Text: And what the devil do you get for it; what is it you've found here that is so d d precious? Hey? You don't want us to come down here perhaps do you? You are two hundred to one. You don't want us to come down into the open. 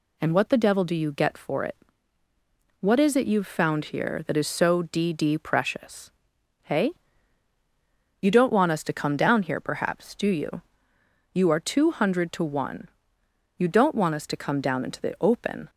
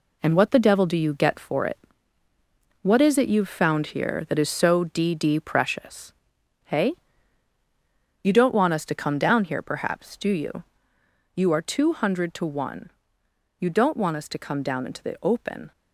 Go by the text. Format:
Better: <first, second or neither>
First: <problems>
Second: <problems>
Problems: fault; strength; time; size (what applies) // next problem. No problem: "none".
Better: first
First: none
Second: gets quieter; throughout; 7 dB